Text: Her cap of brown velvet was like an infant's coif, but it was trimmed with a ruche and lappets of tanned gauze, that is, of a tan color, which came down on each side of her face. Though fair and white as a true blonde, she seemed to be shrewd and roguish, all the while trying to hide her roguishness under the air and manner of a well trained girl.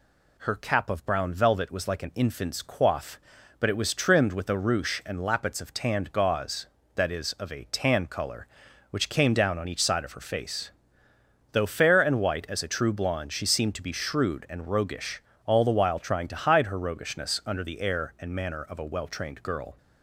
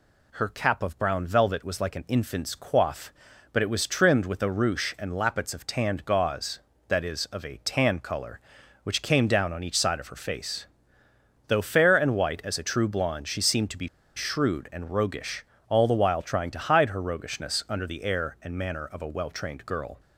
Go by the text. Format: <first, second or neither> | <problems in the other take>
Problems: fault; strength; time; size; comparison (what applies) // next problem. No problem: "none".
first | pauses between "be" and "shrewd"; slight; at 13.8 s; 0.27 s long